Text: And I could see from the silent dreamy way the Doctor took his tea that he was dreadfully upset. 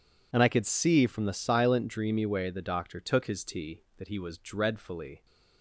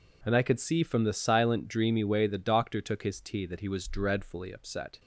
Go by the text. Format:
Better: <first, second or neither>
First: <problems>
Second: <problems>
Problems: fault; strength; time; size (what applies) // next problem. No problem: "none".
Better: second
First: stops before "upset"; at 5.2 s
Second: none